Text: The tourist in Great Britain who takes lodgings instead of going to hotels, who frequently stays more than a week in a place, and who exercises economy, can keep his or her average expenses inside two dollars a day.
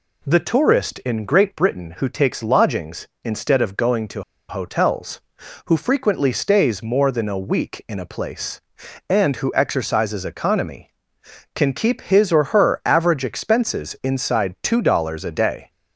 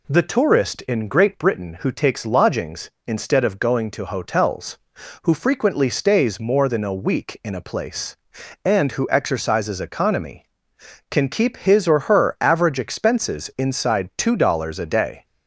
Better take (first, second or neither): second